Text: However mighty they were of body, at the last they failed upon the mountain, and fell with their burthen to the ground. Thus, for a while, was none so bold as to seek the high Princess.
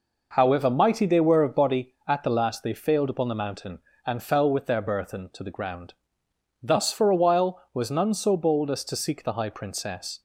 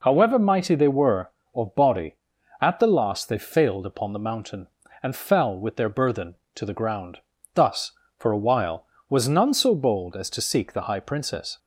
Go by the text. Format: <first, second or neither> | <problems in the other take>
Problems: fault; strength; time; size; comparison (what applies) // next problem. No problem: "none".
neither | none